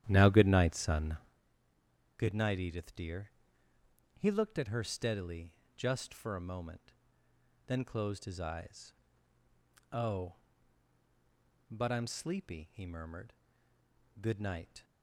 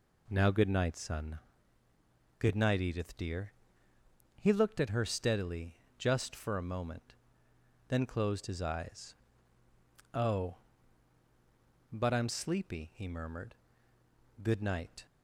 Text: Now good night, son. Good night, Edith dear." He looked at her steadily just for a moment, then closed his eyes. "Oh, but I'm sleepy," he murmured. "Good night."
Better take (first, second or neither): second